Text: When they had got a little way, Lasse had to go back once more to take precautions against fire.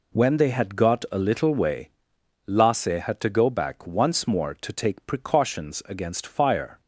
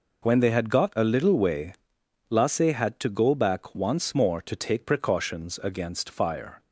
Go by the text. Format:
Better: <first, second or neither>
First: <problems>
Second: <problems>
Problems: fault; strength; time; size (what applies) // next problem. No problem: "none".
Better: neither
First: none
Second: none